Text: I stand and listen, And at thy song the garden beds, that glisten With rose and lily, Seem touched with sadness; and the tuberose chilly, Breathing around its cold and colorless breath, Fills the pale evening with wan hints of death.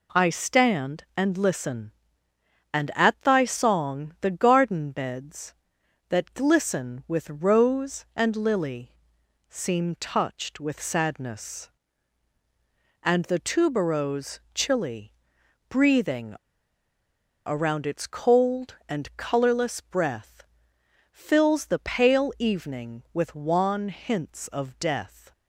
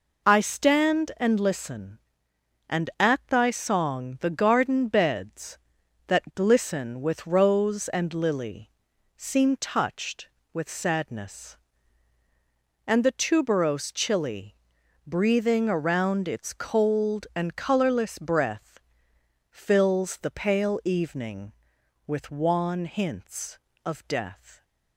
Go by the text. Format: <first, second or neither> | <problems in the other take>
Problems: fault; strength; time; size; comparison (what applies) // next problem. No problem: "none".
second | pauses between "Breathing" and "around"; at 16.3 s; 1.1 s long